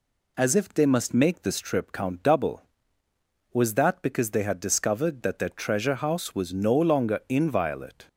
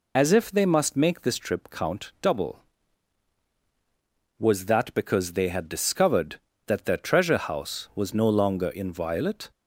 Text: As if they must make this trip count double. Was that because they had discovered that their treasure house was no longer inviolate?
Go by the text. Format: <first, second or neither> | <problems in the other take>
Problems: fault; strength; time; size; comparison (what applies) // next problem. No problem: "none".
first | loses the start of "As"; at 0.1 s; 35 ms